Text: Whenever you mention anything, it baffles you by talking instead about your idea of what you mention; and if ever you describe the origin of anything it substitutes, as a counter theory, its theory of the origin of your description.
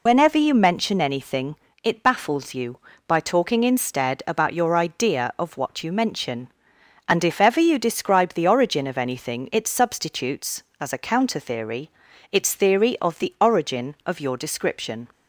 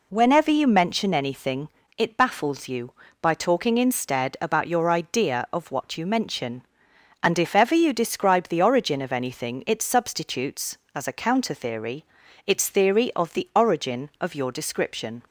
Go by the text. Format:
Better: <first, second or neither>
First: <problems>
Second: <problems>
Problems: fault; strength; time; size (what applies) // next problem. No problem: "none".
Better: second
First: loses the start of "Whenever"; at 0.0 s; 80 ms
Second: none